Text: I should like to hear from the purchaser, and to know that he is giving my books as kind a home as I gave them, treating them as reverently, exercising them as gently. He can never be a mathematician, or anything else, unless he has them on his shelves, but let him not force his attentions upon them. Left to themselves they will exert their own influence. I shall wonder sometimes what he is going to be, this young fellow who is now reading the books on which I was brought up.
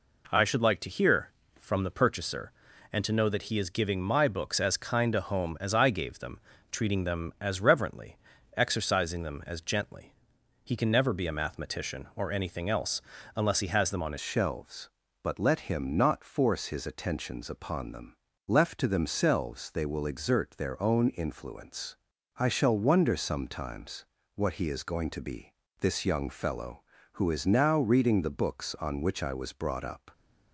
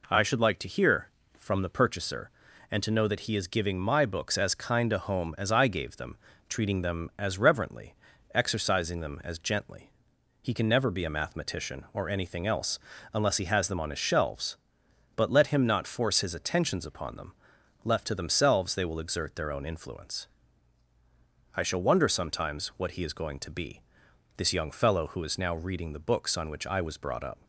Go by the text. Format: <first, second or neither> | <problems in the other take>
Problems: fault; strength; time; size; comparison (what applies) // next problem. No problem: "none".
second | changes voice at "shelves"; from 14.2 s on; 15.9 s long // pauses between "sometimes" and "what"; slight; at 24.0 s; 0.30 s long